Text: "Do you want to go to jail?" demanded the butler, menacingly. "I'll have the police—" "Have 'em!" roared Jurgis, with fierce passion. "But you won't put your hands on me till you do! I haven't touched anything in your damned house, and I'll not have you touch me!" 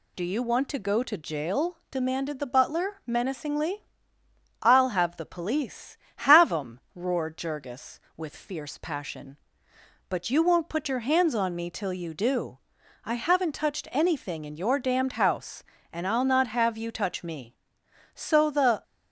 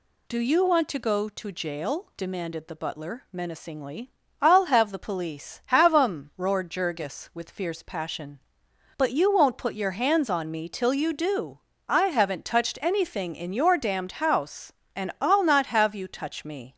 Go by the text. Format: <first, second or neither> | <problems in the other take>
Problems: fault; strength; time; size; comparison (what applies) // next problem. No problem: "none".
second | goes on to say "So the"; noticeable; from 18.1 s on; 0.70 s long